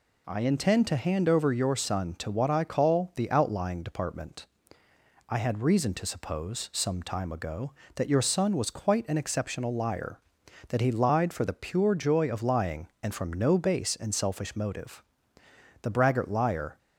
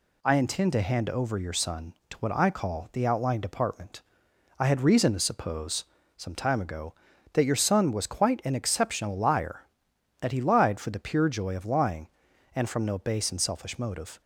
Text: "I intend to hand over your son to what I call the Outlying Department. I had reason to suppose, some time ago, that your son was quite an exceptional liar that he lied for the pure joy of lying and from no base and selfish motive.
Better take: second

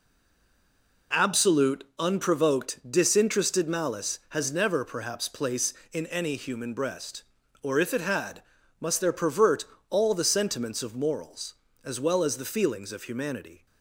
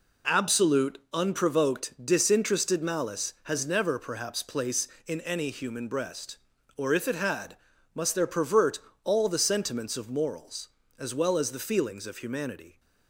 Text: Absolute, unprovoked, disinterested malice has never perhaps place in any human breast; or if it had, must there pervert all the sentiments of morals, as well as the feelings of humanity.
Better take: second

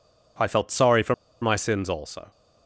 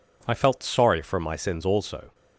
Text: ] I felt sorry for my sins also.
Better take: second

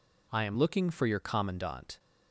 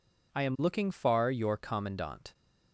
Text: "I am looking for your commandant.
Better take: first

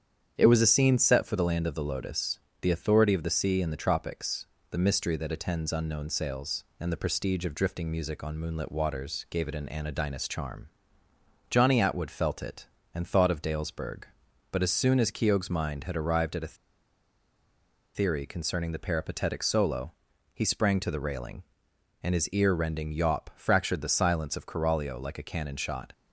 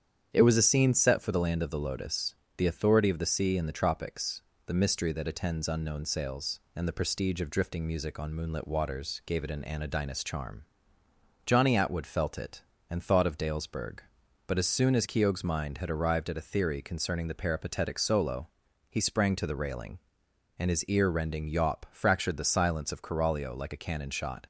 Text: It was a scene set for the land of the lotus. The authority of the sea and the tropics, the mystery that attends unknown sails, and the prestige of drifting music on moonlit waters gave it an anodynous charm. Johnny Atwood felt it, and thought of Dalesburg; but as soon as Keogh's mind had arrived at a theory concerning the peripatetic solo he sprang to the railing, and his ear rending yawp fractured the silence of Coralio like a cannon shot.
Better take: second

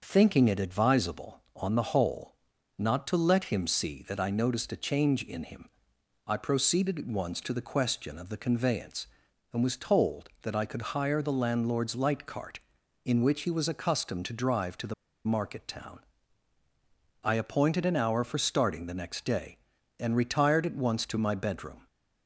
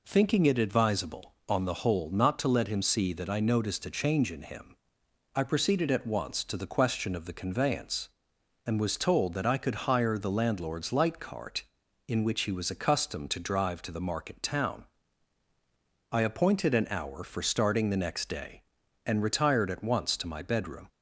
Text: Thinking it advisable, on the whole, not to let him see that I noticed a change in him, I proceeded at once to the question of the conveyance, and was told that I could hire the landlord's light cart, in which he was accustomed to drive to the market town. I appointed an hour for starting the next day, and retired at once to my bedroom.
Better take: second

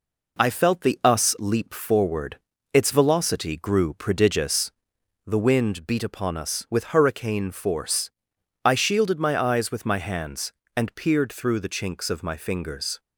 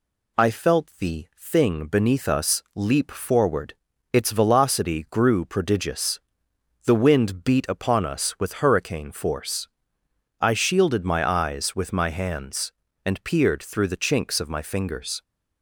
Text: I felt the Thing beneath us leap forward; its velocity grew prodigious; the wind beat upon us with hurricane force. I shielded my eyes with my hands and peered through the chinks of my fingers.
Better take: second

